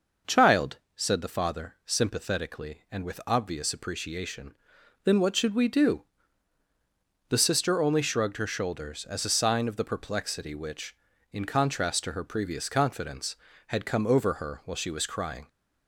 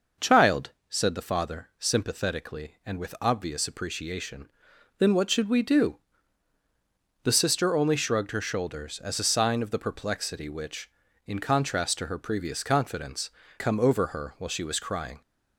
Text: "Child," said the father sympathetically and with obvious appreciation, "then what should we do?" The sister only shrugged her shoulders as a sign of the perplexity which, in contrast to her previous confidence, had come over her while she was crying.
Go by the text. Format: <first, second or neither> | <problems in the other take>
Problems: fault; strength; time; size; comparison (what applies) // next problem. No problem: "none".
first | skips "had"; at 13.4 s